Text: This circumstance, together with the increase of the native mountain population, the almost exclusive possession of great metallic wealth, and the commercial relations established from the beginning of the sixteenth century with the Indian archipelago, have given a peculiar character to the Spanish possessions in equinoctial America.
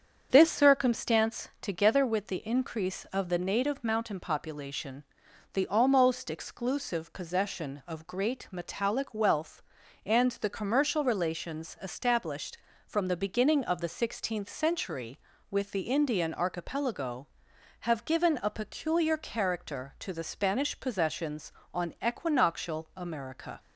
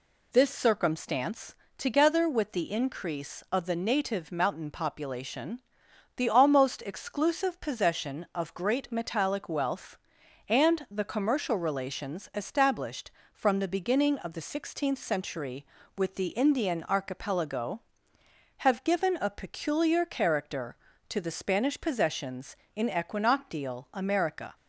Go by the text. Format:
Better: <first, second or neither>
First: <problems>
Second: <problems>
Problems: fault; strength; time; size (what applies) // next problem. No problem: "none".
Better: second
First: starts louder than the rest; strong; until 1.3 s; 7.5 dB // says "on" for "in"; at 21.7 s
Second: none